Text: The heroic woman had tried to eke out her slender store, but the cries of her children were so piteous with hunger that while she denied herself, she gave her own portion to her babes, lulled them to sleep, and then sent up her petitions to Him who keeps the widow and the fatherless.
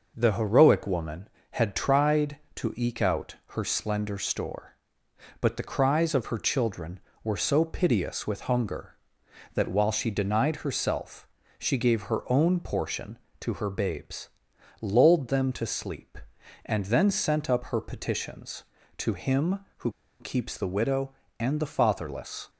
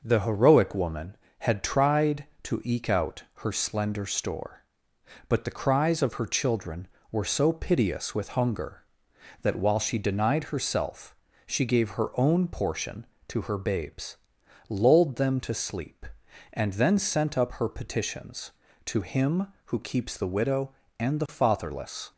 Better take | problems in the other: second | pauses between "who" and "keeps"; slight; at 19.9 s; 0.28 s long

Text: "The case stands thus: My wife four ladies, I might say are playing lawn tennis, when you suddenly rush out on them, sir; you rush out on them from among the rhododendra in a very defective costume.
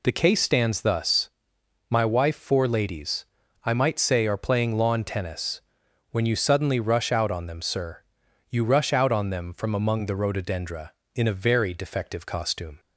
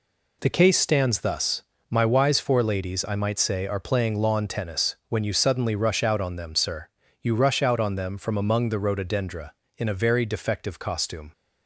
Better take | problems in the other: first | says "wise" for "wife"; at 2.0 s

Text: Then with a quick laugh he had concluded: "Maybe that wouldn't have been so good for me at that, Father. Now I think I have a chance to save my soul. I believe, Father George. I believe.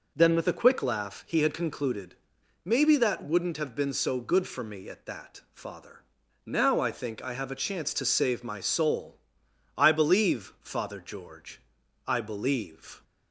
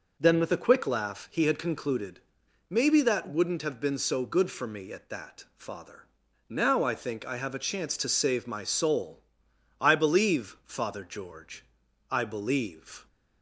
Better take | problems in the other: neither | none

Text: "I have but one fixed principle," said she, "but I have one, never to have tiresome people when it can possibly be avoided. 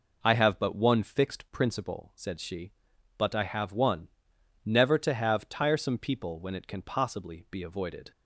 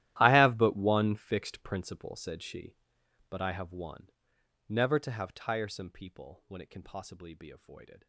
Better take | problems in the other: first | gets quieter; strong; throughout; 20 dB

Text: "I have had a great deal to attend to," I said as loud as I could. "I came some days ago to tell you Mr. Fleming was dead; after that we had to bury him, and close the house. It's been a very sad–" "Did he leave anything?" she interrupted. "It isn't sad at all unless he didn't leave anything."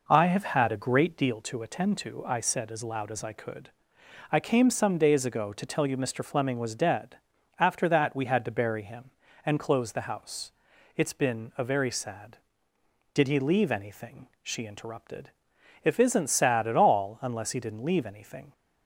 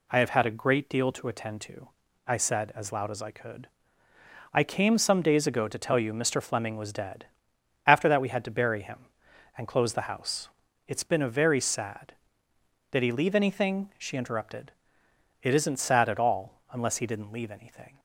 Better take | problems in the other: second | says "If" for "It"; at 15.8 s

